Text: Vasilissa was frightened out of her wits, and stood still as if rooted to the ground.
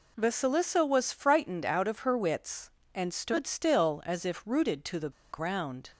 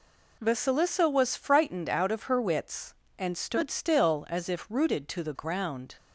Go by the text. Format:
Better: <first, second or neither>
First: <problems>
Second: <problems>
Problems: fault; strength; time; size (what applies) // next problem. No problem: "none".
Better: second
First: pauses between "the" and "ground"; slight; at 5.1 s; 0.21 s long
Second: none